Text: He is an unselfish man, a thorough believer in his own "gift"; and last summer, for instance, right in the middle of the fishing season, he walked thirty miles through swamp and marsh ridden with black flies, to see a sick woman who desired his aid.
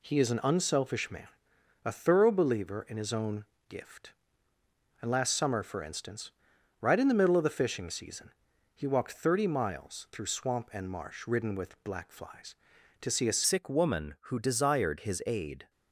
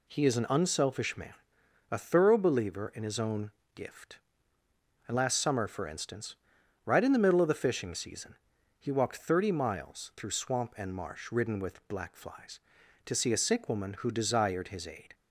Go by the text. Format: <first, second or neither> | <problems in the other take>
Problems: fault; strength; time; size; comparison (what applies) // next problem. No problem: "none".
second | pauses between "own" and "gift"; slight; at 3.4 s; 0.24 s long; slight in the second // changes voice at "sick"; from 13.4 s on; 2.2 s long